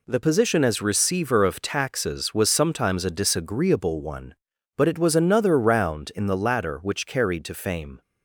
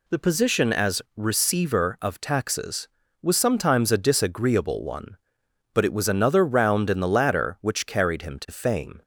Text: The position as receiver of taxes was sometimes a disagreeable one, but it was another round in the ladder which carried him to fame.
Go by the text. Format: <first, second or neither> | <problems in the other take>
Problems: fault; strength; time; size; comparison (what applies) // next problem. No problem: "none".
second | skips "him"; at 7.4 s